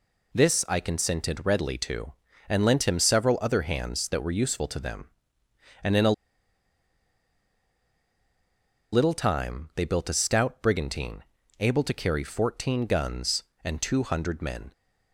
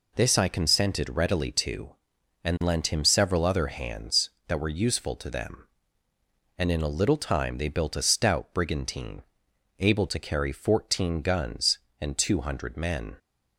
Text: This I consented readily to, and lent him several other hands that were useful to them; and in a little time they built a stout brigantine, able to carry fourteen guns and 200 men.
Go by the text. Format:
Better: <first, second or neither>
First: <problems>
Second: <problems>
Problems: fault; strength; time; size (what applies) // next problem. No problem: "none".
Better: second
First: pauses between "a" and "little"; strong; at 6.1 s; 2.8 s long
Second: none